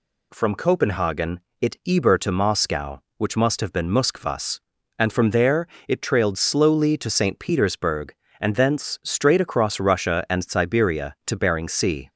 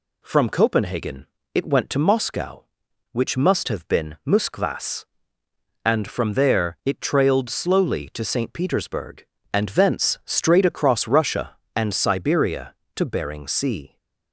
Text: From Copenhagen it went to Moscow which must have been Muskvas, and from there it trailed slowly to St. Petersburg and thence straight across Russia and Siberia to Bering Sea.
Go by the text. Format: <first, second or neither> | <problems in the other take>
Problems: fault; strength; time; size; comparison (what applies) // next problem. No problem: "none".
second | pauses between "Copenhagen" and "it"; slight; at 1.3 s; 0.22 s long; slight in the second // says "eber" for "went"; at 1.8 s // pauses between "there" and "it"; slight; at 5.6 s; 0.22 s long